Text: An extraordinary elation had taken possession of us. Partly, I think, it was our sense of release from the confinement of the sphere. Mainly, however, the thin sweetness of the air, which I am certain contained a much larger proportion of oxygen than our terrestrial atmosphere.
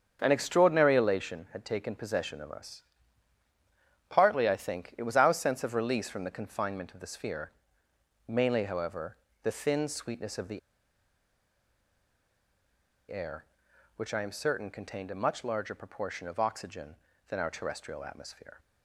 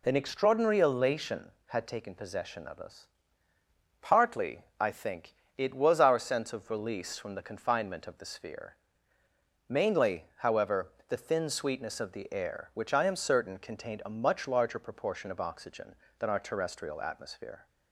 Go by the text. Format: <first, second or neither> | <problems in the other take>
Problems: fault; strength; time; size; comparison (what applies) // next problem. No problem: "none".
second | starts louder than the rest; strong; until 1.2 s; 7 dB // pauses between "the" and "air"; strong; at 10.5 s; 2.5 s long